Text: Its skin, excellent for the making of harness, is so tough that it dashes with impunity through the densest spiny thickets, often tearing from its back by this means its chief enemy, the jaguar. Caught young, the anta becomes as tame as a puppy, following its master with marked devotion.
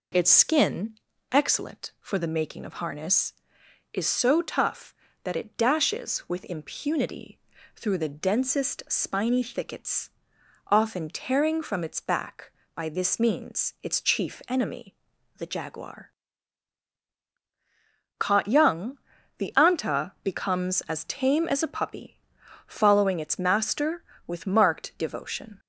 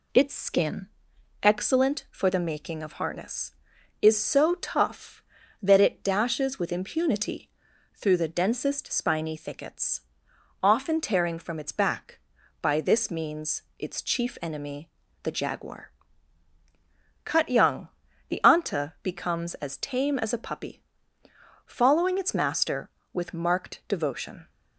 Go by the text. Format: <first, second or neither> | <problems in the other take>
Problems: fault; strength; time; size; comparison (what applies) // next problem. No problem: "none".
first | pauses between "impunity" and "through"; noticeable; at 7.4 s; 0.46 s long; slight in the first // pauses between "means" and "its"; slight; at 13.6 s; 0.16 s long // says "Cut" for "Caught"; at 17.2 s